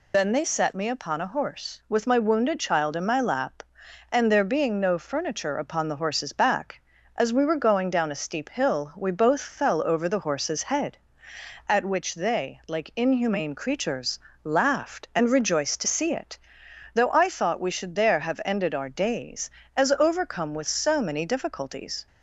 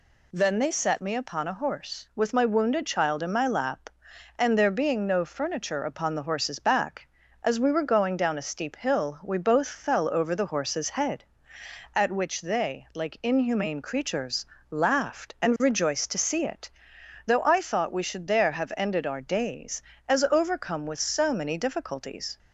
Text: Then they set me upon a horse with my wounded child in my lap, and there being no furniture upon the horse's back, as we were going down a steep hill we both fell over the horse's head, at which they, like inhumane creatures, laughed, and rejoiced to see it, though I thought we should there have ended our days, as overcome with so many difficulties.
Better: second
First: loses the start of "Then"; at 0.1 s; 85 ms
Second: none

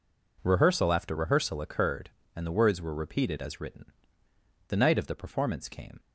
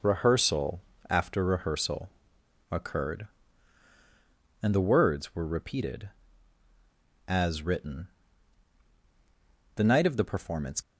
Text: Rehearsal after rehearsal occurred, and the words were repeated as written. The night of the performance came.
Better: first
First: none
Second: pauses between "Rehearsal" and "after"; slight; at 0.8 s; 0.30 s long // pauses between "rehearsal" and "occurred"; noticeable; at 2.0 s; 0.62 s long // stops before "came"; at 10.8 s

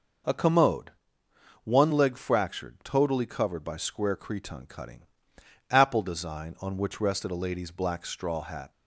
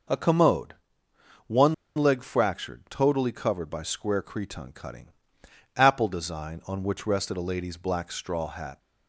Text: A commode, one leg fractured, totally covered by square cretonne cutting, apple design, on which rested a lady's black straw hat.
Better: first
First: none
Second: pauses between "one" and "leg"; slight; at 1.7 s; 0.22 s long

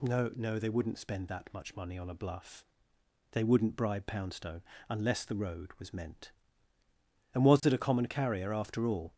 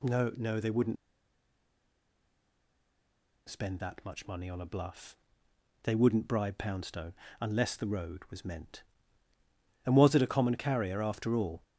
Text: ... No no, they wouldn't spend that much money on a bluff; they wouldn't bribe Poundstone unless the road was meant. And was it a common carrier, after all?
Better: first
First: pauses between "Poundstone" and "unless"; slight; at 4.6 s; 0.26 s long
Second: pauses between "wouldn't" and "spend"; strong; at 0.9 s; 2.5 s long // pauses between "Poundstone" and "unless"; slight; at 7.1 s; 0.26 s long

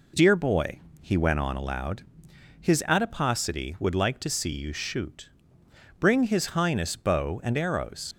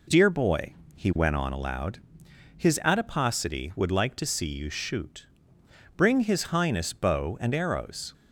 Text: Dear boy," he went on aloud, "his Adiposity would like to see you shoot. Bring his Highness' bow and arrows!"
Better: second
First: leaves "arrows" unfinished; at 8.1 s; 45 ms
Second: none

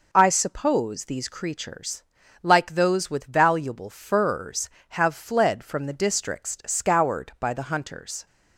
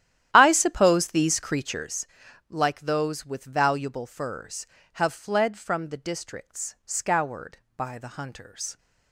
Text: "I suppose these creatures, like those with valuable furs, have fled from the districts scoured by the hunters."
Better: first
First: none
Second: starts louder than the rest; strong; until 2.1 s; 11.5 dB

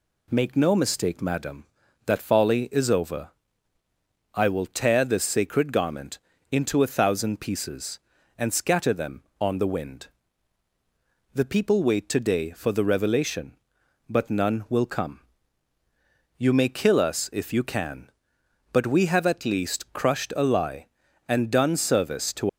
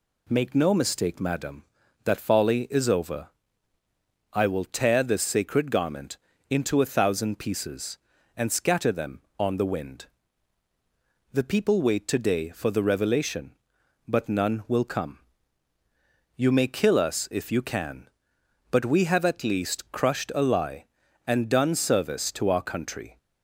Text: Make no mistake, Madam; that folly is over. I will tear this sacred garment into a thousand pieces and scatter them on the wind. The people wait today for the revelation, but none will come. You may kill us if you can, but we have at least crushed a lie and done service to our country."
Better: second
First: pauses between "garment" and "into"; slight; at 6.1 s; 0.32 s long // stops before "our country"; at 22.4 s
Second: pauses between "garment" and "into"; slight; at 6.1 s; 0.32 s long

